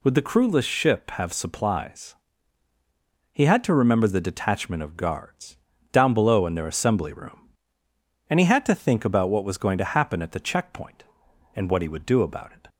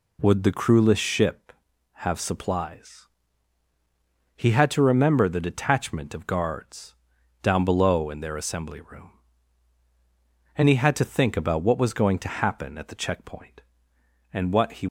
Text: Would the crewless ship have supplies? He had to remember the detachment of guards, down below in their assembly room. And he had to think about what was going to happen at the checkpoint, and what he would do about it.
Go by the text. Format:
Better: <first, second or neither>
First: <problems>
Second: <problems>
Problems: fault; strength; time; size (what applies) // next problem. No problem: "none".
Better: first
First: none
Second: stops before "would do about it"; at 14.8 s